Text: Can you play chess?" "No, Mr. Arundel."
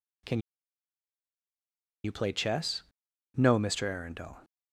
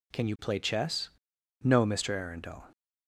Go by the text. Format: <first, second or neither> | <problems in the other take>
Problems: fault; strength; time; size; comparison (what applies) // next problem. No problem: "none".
second | pauses between "Can" and "you"; strong; at 0.3 s; 1.6 s long